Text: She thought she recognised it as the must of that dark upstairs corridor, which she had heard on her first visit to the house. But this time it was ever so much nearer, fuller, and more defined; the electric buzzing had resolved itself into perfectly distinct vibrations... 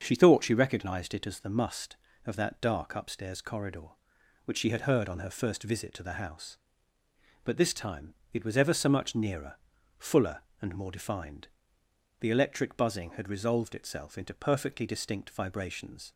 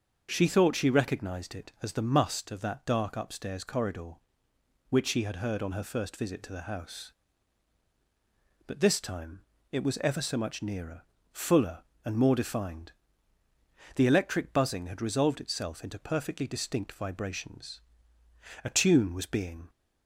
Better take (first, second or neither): first